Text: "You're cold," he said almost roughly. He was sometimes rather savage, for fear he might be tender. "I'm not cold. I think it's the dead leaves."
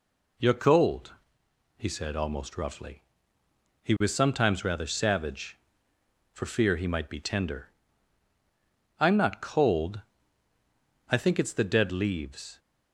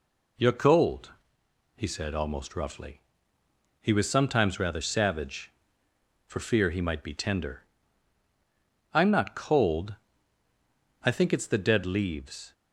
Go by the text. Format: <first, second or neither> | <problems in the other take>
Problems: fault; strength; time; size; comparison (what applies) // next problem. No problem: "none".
neither | none